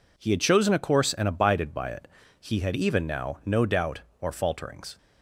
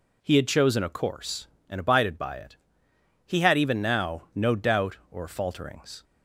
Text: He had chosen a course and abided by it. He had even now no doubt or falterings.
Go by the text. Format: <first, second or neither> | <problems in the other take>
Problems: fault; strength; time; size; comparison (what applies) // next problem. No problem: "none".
neither | none